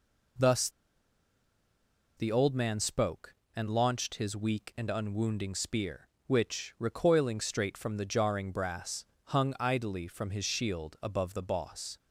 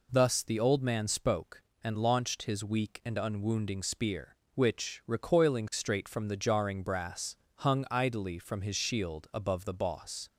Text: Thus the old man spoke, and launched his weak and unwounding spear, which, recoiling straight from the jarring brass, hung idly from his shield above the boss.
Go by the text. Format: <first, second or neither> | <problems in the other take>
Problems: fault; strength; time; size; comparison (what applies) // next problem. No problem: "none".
second | pauses between "Thus" and "the"; strong; at 0.6 s; 1.4 s long